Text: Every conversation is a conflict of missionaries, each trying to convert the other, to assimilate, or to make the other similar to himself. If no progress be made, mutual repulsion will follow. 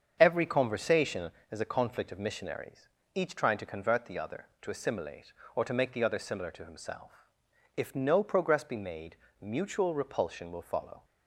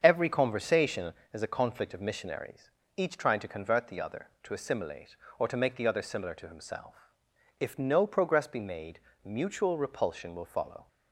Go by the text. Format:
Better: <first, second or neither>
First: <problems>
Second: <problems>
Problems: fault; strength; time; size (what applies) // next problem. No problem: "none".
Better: neither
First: starts louder than the rest; until 1.2 s; 7 dB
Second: starts louder than the rest; until 1.0 s; 7 dB